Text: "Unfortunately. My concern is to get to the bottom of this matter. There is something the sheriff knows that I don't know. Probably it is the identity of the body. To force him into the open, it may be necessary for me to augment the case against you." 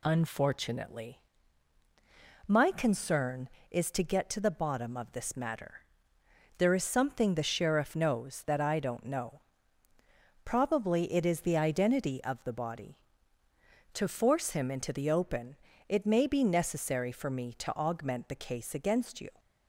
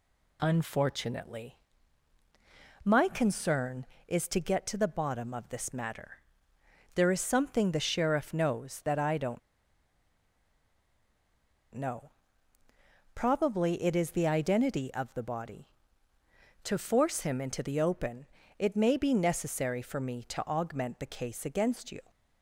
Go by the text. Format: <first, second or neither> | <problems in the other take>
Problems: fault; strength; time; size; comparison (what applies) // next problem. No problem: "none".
first | pauses between "don't" and "know"; strong; at 9.3 s; 2.3 s long